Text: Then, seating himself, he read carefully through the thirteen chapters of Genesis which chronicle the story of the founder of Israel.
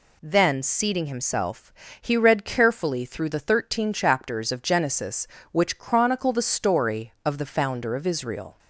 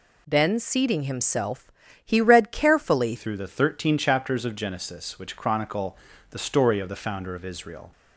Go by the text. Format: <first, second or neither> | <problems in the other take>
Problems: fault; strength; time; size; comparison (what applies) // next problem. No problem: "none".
first | changes voice at "through"; from 3.1 s on; 4.8 s long // pauses between "chronicle" and "the"; slight; at 5.9 s; 0.34 s long